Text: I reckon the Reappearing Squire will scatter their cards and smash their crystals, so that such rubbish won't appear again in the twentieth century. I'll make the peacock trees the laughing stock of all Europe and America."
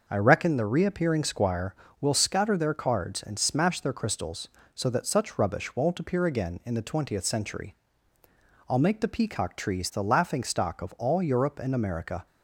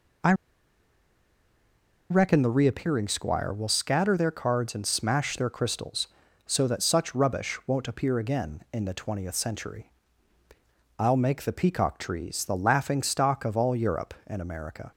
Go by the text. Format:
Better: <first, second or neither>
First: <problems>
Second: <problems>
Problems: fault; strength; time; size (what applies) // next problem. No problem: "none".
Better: first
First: none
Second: pauses between "I" and "reckon"; strong; at 0.3 s; 1.7 s long